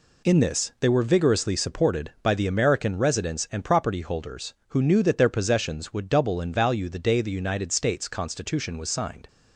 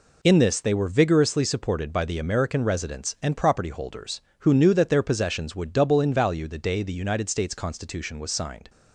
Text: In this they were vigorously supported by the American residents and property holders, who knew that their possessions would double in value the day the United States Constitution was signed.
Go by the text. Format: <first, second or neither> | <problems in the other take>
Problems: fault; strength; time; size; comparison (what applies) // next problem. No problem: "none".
neither | none